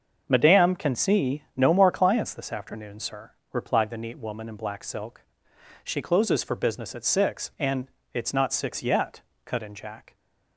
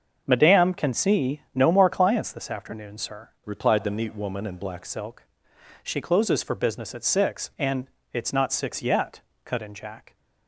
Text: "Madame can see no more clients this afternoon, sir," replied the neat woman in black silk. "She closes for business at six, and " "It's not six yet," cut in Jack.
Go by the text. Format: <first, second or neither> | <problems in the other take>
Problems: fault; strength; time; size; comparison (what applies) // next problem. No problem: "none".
first | starts louder than the rest; until 1.2 s; 6.5 dB; also in the first // changes voice from "replied" to "black"; from 3.4 to 4.8 s; 1.4 s long